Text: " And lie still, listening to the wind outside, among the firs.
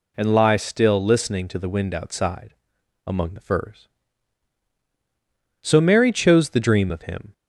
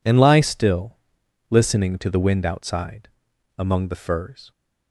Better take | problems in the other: second | goes on to say "So Mary chose the dream of Him"; strong; from 5.6 s on; 1.7 s long

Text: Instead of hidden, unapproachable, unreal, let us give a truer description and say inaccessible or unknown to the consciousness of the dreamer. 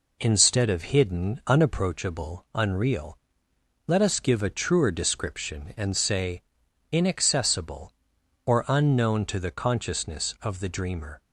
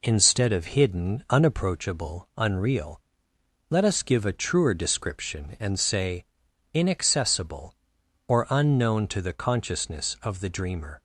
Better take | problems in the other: neither | pauses between "say" and "inaccessible"; noticeable; the same in both

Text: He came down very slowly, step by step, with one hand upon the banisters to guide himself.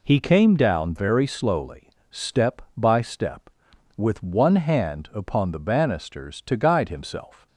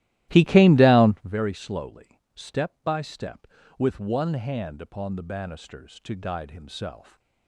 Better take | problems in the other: first | starts louder than the rest; strong; until 1.3 s; 15.5 dB

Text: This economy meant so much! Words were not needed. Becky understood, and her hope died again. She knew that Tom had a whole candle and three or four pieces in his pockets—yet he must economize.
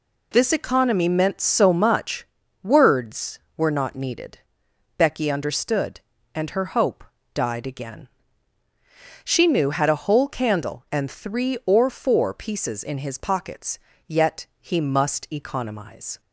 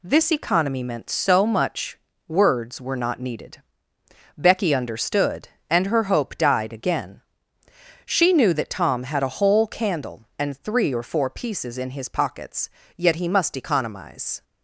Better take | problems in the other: second | pauses between "hope" and "died"; slight; at 7.0 s; 0.31 s long // skips "that Tom"; at 9.7 s

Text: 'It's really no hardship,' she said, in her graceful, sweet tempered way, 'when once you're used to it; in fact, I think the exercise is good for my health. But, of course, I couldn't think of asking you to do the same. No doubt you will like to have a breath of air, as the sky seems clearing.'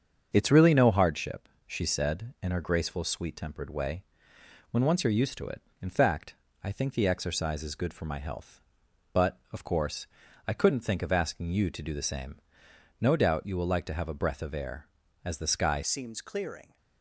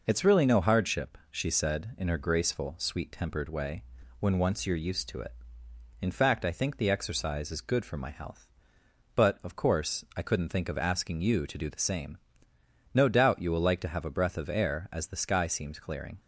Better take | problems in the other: second | starts louder than the rest; until 1.3 s; 7 dB // changes voice at "seems"; from 15.8 s on; 0.9 s long

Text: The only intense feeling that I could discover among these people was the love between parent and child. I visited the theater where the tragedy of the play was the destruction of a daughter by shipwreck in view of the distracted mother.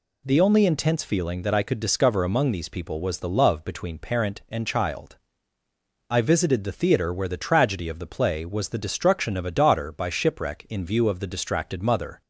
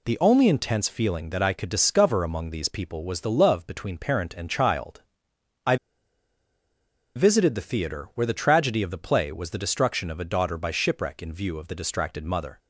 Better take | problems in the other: first | pauses between "I" and "visited"; strong; at 5.7 s; 1.4 s long

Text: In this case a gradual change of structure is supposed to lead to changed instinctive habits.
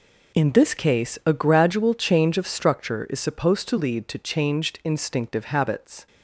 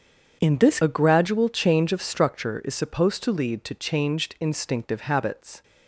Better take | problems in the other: first | starts louder than the rest; strong; until 1.4 s; 7.5 dB // skips "case"; at 0.8 s

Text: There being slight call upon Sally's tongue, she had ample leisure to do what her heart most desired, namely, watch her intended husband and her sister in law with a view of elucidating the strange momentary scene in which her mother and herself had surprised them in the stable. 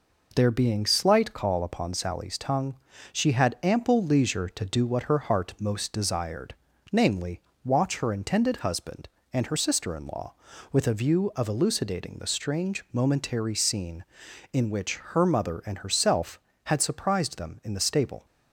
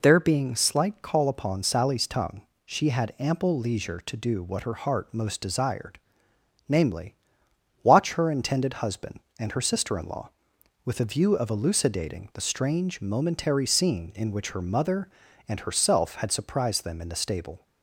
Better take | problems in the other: neither | none

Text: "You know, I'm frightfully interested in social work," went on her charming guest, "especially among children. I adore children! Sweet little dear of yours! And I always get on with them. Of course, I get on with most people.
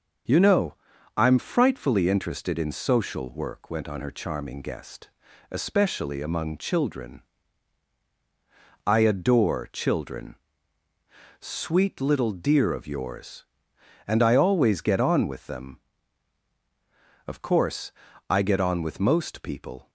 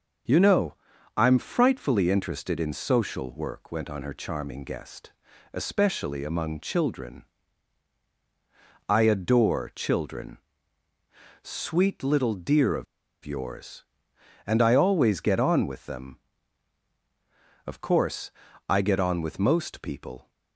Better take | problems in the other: first | starts louder than the rest; until 1.6 s; 6.5 dB; also in the first // pauses between "of" and "yours"; at 12.8 s; 0.39 s long

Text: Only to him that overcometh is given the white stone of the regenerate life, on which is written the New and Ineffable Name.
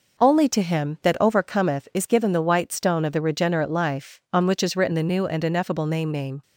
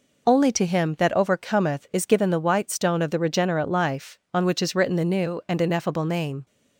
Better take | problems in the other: second | says "Name" twice; at 6.0 s

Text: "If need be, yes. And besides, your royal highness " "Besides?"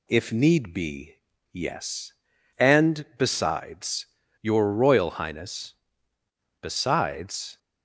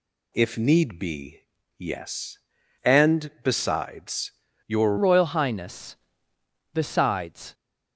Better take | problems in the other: first | changes voice at "royal"; from 4.9 s on; 2.6 s long

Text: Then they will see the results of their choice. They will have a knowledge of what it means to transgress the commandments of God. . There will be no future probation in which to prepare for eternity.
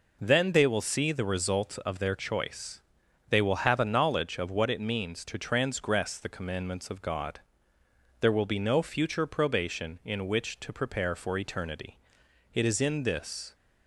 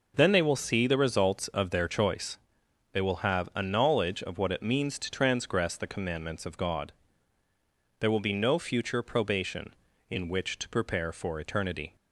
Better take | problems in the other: second | goes on to say "It is in this"; noticeable; from 12.5 s on; 1.0 s long

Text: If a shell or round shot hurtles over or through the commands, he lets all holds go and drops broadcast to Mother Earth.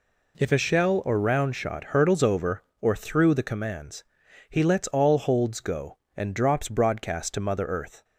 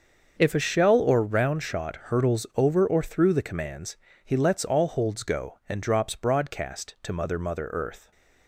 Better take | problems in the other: first | starts louder than the rest; until 1.4 s; 6.5 dB // says "Mother" twice; at 7.3 s

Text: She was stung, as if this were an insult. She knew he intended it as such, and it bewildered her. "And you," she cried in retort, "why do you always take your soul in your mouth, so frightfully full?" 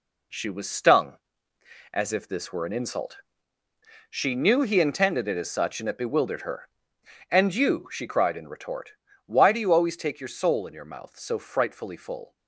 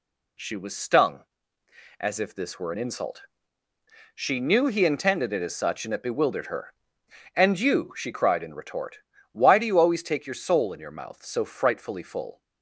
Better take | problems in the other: second | gets quieter; throughout; 6.5 dB

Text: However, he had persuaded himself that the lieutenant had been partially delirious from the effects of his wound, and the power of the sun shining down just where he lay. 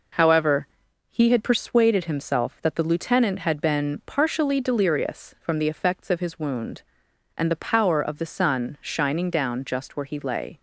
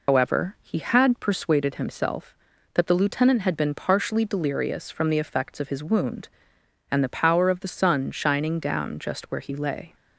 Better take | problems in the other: first | loses the start of "However"; at 0.0 s; 120 ms

